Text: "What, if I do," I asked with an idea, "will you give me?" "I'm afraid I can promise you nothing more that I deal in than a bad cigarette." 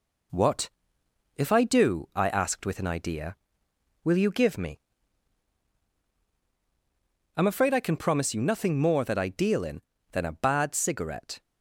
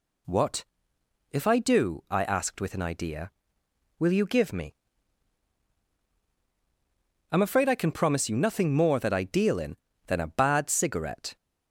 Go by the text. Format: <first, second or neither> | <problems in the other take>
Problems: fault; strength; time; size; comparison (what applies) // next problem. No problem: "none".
second | gets quieter; slight; throughout; 2.5 dB